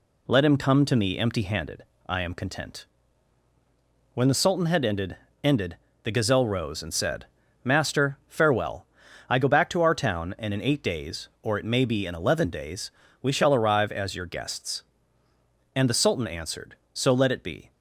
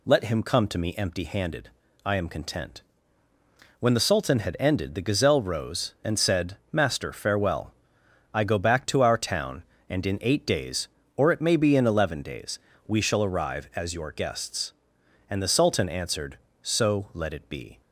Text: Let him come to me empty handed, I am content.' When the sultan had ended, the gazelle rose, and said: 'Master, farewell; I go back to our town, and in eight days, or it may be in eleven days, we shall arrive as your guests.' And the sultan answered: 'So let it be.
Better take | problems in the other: second | says "ended" twice; at 5.4 s

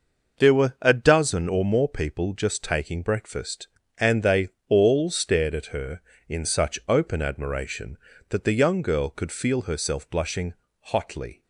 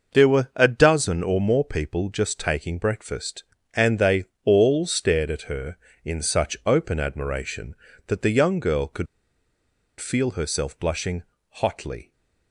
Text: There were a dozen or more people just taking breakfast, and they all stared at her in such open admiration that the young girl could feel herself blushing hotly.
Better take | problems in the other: first | pauses between "they" and "all"; slight; at 4.2 s; 0.20 s long; slight in the first // pauses between "could" and "feel"; noticeable; at 9.0 s; 0.94 s long // pauses between "blushing" and "hotly"; slight; at 11.2 s; 0.28 s long; slight in the first

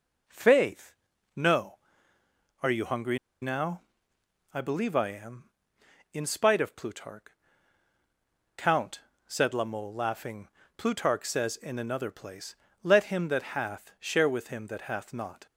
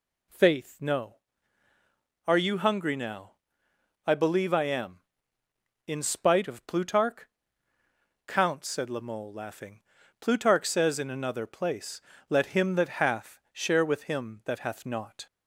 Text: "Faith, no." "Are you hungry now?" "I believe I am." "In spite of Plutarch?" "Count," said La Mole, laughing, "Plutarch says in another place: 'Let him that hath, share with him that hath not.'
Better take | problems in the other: second | pauses between "hungry" and "now"; slight; at 3.1 s; 0.25 s long

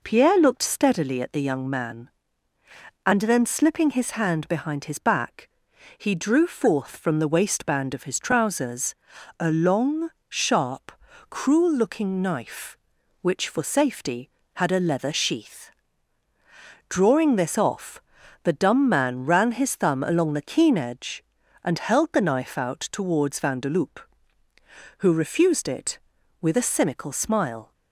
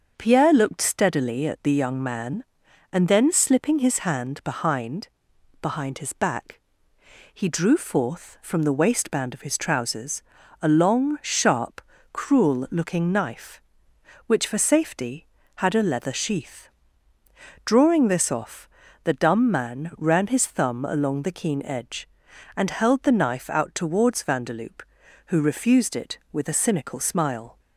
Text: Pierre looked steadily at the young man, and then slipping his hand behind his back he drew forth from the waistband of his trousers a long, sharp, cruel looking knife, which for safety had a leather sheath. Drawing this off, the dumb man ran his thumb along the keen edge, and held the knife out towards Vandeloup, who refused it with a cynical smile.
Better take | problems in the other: first | starts louder than the rest; until 1.1 s; 6.5 dB // says "behind" twice; at 5.6 s // pauses between "back" and "he"; noticeable; at 6.6 s; 0.72 s long; noticeable in the first // pauses between "trousers" and "a"; at 10.2 s; 0.38 s long; also in the first

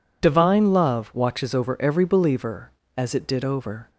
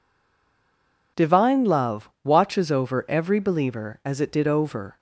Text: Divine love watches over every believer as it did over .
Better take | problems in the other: first | stays silent before the first word; until 1.1 s; 1.1 s long

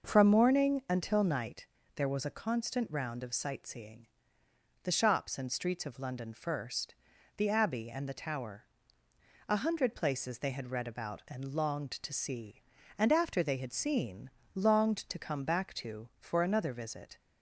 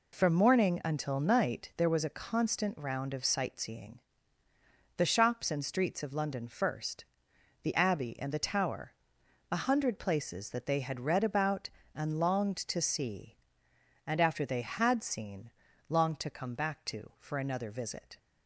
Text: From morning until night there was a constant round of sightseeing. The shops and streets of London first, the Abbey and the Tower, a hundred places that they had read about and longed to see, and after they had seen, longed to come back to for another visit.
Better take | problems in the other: second | pauses between "night" and "there"; slight; at 1.6 s; 0.30 s long // skips "that"; at 10.3 s

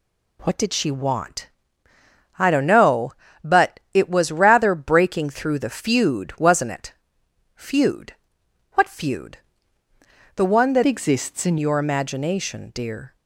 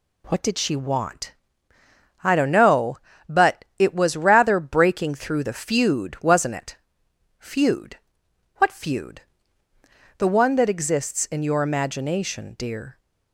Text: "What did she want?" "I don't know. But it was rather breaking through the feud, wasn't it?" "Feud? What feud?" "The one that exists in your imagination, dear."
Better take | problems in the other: second | changes voice from "exists" to "in"; from 10.8 to 11.5 s; 0.7 s long

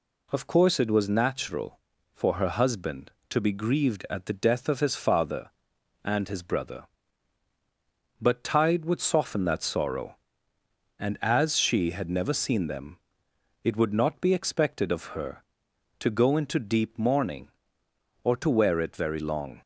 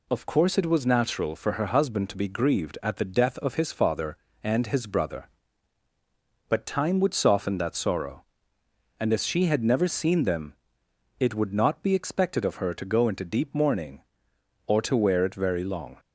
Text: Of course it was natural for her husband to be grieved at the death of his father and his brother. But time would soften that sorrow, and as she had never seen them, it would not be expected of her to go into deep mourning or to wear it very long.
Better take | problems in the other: second | says "tide" for "time"; at 8.4 s

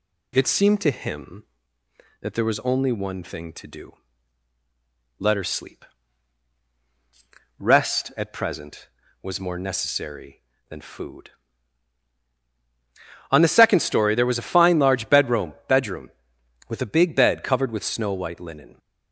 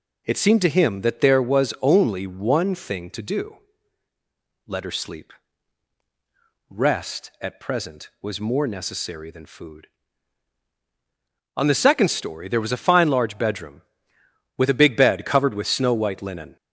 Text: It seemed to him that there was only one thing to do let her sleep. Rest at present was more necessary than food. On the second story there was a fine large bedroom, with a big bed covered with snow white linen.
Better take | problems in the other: second | pauses between "do" and "let"; strong; at 3.9 s; 1.2 s long; also in the second // says "bedroom" twice; at 15.6 s

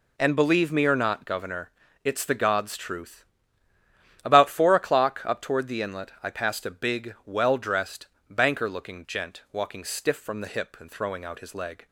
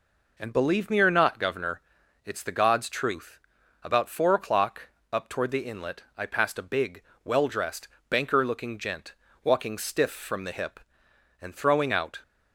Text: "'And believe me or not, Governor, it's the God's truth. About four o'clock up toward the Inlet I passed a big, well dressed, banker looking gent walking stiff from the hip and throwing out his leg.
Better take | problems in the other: first | pauses between "o'clock" and "up"; slight; at 4.8 s; 0.24 s long // pauses between "gent" and "walking"; slight; at 9.1 s; 0.32 s long // stops before "his leg"; at 12.2 s

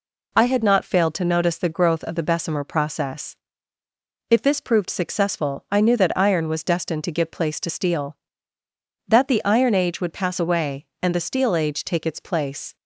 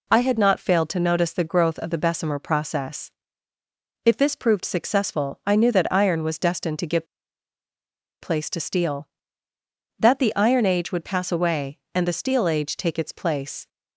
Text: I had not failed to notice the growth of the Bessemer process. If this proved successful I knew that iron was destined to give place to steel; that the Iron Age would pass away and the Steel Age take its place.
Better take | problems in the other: first | pauses between "give" and "place"; at 7.0 s; 1.1 s long

